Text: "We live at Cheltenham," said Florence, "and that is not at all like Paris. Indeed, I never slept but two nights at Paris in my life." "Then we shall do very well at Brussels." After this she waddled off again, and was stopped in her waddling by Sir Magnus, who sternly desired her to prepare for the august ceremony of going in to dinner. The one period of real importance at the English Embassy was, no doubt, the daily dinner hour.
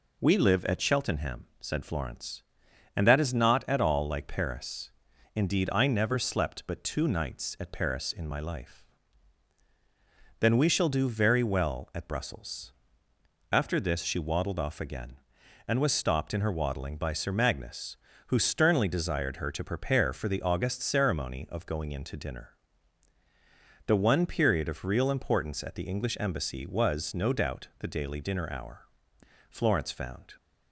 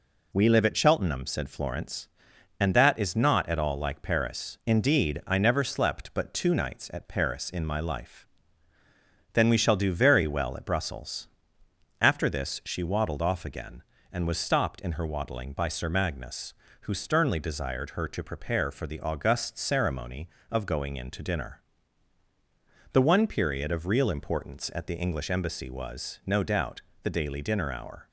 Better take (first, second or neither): second